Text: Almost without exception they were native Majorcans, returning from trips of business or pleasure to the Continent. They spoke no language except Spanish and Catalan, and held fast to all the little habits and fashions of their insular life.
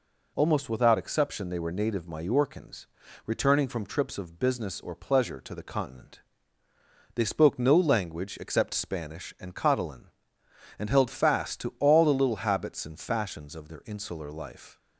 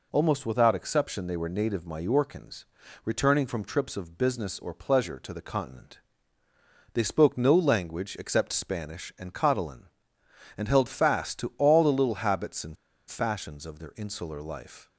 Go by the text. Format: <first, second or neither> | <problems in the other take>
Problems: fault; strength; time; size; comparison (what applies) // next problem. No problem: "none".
first | pauses between "and" and "fashions"; slight; at 12.7 s; 0.32 s long